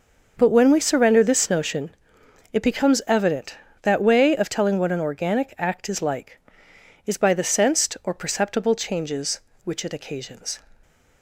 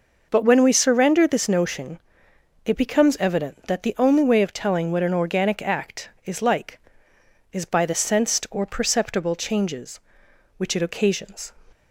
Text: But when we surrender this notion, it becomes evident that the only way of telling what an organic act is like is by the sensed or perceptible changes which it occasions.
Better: second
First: starts louder than the rest; noticeable; until 1.3 s; 6 dB // skips "the only"; at 4.0 s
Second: none

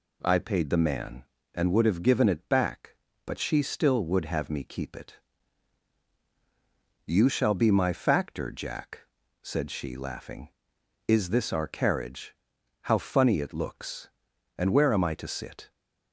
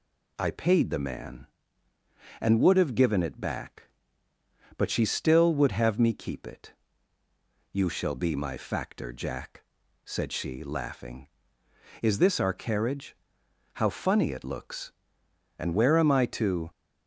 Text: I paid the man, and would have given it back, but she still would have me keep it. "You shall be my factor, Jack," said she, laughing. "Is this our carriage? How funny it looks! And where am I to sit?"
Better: first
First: none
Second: stops before "sit"; at 16.7 s

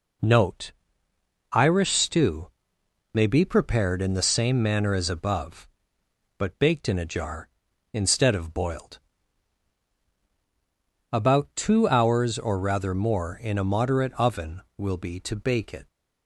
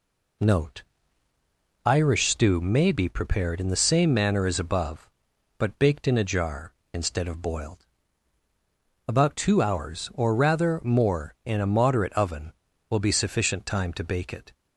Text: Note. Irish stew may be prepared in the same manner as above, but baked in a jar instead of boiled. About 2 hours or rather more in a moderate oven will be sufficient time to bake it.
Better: second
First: pauses between "stew" and "may"; noticeable; at 2.5 s; 0.64 s long // skips "sufficient time"; at 15.1 s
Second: none

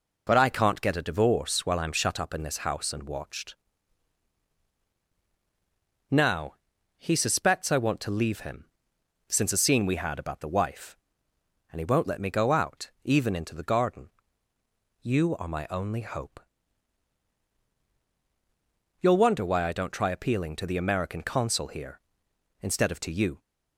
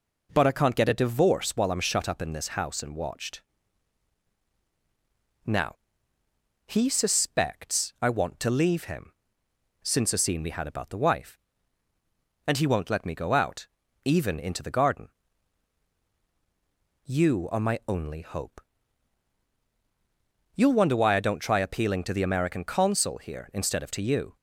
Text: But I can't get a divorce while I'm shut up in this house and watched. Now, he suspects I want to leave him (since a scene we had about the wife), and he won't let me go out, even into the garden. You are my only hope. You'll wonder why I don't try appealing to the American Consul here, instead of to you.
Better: neither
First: none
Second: none

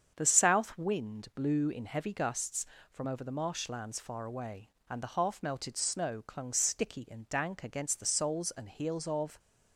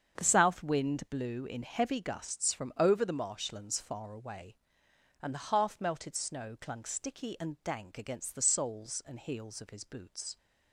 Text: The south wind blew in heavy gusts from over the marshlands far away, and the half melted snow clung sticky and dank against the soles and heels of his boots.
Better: second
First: starts louder than the rest; strong; until 1.1 s; 7.5 dB // stops before "his boots"; at 9.3 s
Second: starts louder than the rest; strong; until 1.2 s; 7.5 dB

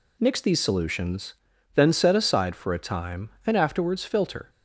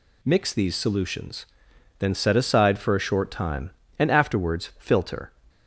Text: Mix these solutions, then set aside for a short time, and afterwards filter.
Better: second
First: skips "short"; at 2.7 s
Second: none

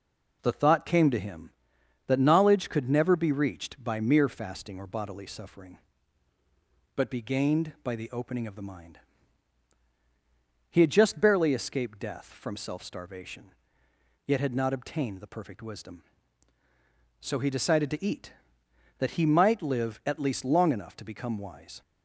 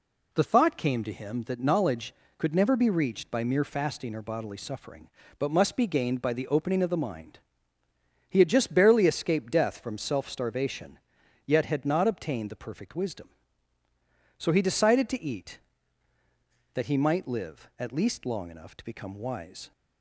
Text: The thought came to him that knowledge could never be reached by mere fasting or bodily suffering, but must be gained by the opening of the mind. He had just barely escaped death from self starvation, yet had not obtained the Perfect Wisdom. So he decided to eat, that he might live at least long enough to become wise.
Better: second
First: skips "must"; at 7.0 s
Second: none

